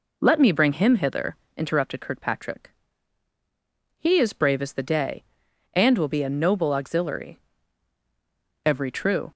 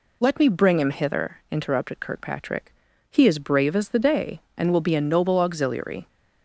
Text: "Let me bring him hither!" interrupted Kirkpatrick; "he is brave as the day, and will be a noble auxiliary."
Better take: second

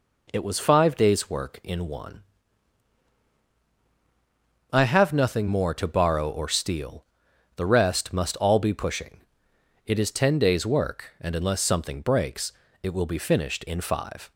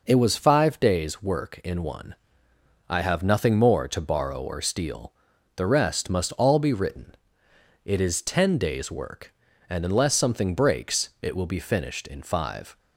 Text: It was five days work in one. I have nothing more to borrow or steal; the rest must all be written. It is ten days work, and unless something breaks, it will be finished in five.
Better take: second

